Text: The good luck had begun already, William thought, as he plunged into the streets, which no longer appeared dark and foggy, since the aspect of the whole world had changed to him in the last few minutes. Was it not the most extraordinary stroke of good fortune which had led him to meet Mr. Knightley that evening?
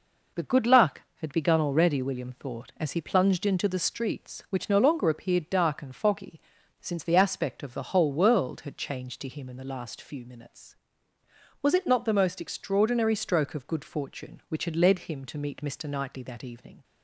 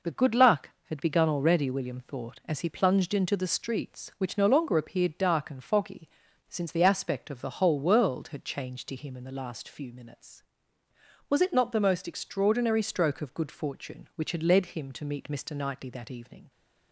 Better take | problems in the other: neither | none

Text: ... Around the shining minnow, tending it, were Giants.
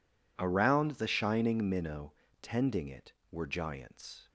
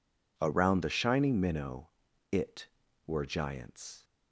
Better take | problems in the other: first | skips "tending"; at 2.0 s

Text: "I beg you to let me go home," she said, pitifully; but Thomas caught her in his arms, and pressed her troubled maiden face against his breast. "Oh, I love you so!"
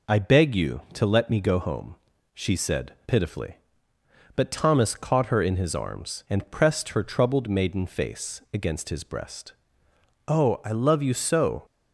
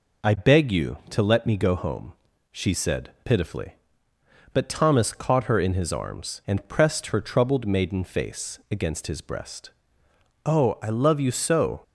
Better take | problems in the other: neither | none

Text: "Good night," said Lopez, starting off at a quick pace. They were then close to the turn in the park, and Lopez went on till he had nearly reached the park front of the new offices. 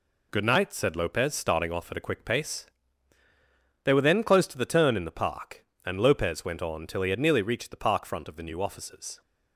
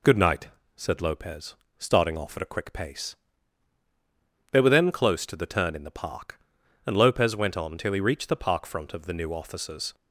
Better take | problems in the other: first | skips "had nearly"; at 8.0 s

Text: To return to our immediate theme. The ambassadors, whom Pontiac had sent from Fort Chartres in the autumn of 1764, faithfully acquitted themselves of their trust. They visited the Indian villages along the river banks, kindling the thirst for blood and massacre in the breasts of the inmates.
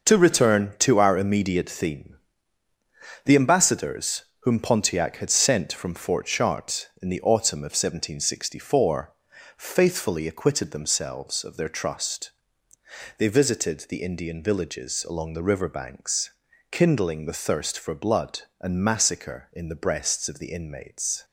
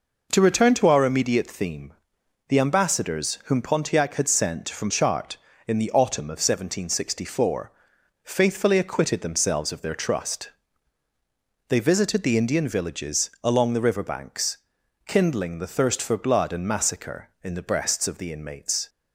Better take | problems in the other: first | skips "Fort"; at 4.8 s

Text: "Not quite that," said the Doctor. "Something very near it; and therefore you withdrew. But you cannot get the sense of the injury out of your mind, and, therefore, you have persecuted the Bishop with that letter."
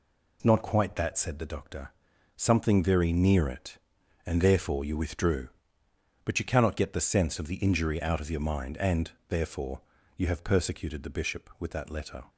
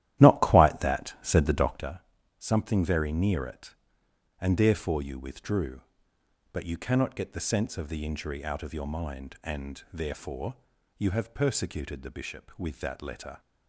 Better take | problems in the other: first | starts louder than the rest; strong; until 1.9 s; 13 dB

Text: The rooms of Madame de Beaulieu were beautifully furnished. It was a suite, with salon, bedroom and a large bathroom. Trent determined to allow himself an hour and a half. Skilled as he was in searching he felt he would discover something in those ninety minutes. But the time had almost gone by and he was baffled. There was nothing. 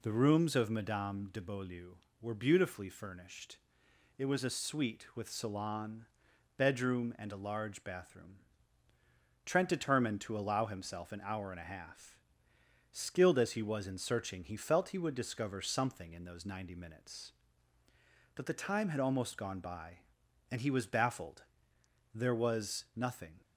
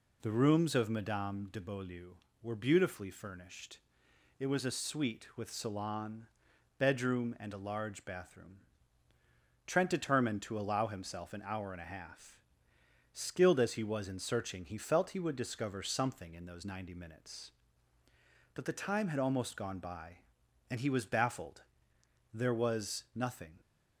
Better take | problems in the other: neither | none

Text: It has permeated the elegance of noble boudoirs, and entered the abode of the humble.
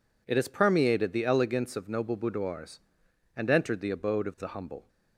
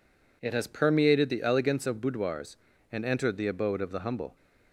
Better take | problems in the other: first | skips "noble"; at 2.0 s

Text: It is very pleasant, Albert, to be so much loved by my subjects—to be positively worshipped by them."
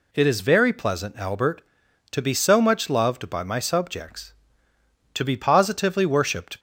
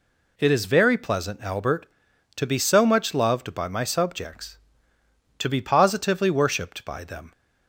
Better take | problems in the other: second | stops before "by them"; at 6.5 s

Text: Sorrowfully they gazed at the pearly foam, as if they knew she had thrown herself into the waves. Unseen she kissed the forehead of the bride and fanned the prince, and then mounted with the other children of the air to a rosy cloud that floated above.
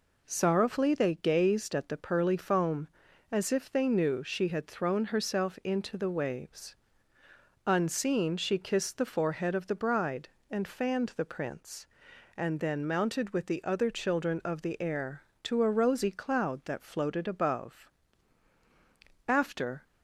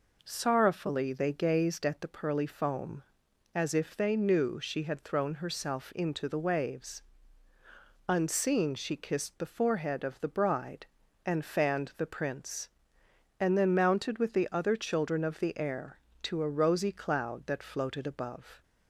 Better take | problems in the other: second | goes on to say "After"; from 19.2 s on; 0.56 s long

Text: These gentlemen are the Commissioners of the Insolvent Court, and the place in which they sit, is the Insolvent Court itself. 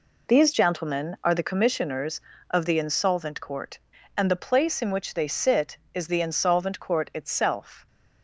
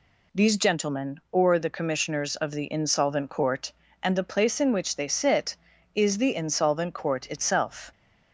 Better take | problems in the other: first | says "or" for "are"; at 1.3 s

